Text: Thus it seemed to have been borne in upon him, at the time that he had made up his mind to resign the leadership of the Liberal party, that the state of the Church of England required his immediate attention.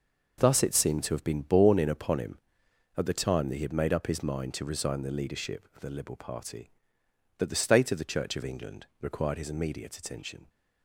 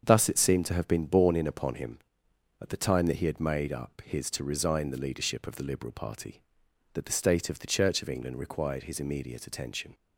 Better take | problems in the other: first | starts louder than the rest; until 1.0 s; 7 dB // skips "mind"; at 4.3 s

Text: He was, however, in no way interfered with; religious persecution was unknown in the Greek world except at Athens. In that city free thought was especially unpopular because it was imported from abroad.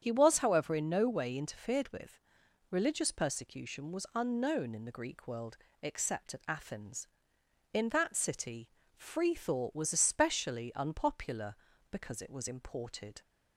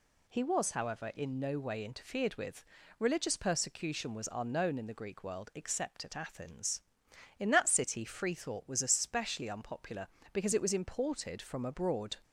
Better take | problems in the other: second | starts louder than the rest; strong; until 1.0 s; 8.5 dB // pauses between "world" and "except"; slight; at 5.5 s; 0.26 s long // pauses between "city" and "free"; slight; at 8.6 s; 0.30 s long // stops before "from abroad"; at 13.2 s

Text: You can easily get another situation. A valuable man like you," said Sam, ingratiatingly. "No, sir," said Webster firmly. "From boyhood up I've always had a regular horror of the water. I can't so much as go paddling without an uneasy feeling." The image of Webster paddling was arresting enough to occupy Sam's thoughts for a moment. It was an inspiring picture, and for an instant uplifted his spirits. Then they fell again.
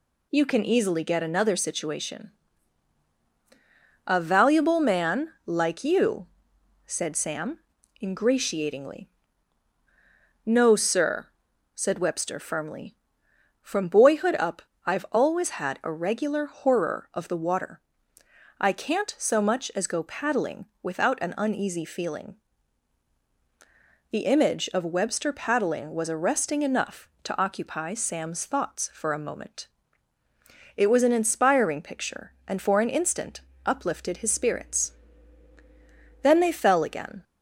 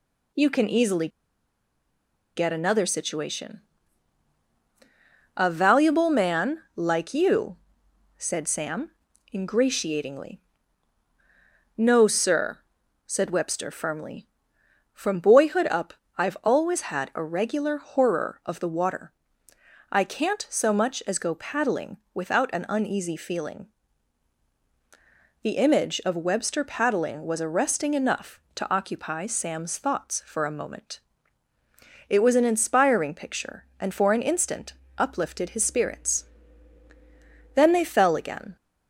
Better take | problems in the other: first | pauses between "easily" and "get"; strong; at 1.0 s; 1.2 s long // pauses between "man" and "like"; slight; at 6.5 s; 0.16 s long; slight in the first // pauses between "up" and "I've"; slight; at 15.9 s; 0.22 s long; slight in the first // pauses between "paddling" and "without"; slight; at 21.9 s; 0.16 s long; slight in the first // pauses between "instant" and "uplifted"; slight; at 34.7 s; 0.24 s long; slight in the first

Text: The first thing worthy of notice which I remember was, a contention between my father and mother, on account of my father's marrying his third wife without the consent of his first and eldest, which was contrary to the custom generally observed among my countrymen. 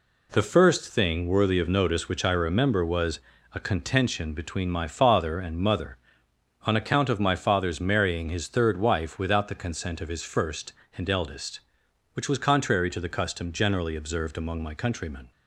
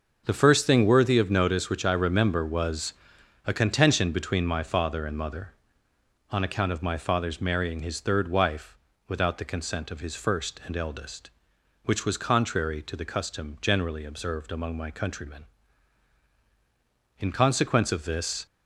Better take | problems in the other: first | starts louder than the rest; noticeable; until 1.2 s; 6 dB // pauses between "wife" and "without"; slight; at 8.7 s; 0.32 s long // goes on to say "In consequence of this"; noticeable; from 17.1 s on; 1.2 s long

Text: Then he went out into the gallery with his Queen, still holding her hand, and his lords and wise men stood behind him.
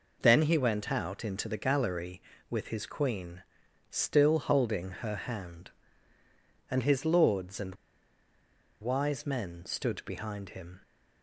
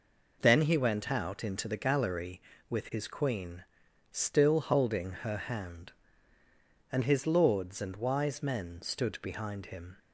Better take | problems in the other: second | pauses between "and" and "wise"; at 7.7 s; 1.0 s long

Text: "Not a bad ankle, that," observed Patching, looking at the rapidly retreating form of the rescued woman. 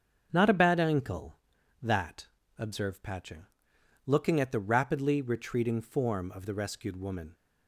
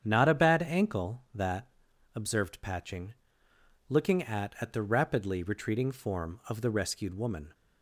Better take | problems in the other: first | starts louder than the rest; strong; until 1.0 s; 8.5 dB; also in the first // says "at" twice; at 4.5 s

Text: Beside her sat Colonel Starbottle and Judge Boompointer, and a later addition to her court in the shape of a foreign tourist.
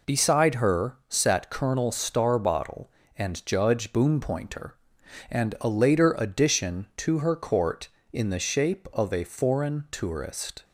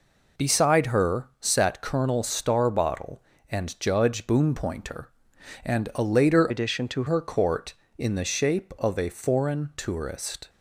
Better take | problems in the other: first | changes voice from "addition" to "to"; from 6.4 to 7.0 s; 0.6 s long

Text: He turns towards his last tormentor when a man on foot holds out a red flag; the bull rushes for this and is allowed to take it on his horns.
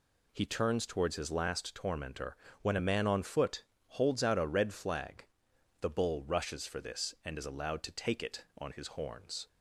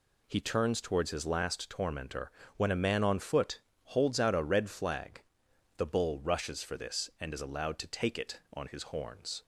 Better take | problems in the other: neither | pauses between "tormentor" and "when"; slight; the same in both // pauses between "foot" and "holds"; slight; the same in both

